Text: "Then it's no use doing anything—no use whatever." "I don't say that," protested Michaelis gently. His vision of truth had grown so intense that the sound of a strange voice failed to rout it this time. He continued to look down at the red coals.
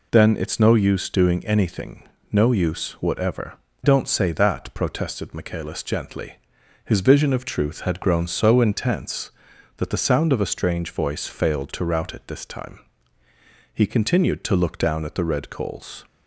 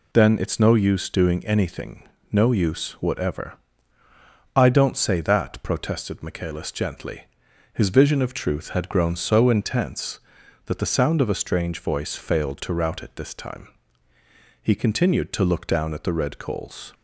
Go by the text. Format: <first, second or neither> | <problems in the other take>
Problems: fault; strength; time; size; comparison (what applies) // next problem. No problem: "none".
second | skips "I"; at 3.7 s